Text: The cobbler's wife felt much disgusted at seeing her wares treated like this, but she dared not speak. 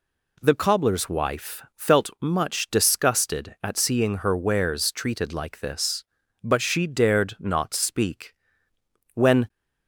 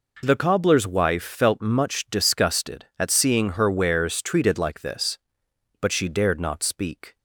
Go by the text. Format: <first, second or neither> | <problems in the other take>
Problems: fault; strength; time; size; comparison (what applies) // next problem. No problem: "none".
second | goes on to say "When"; slight; from 9.1 s on; 0.34 s long